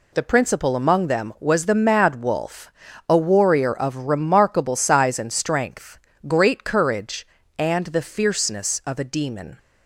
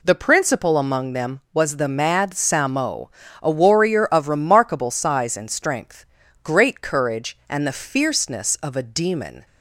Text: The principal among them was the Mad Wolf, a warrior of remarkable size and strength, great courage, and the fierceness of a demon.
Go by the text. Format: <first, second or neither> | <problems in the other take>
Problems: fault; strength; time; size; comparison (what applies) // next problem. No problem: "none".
first | says "Samo" for "Wolf"; at 2.3 s